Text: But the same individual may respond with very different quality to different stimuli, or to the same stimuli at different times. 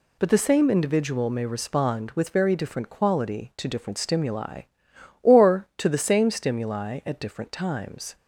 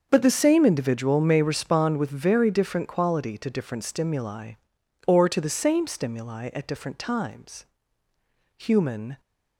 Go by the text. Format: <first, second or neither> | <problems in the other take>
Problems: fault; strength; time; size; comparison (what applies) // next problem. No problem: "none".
first | starts louder than the rest; until 1.1 s; 6.5 dB // goes on to say "Human"; noticeable; from 8.5 s on; 0.62 s long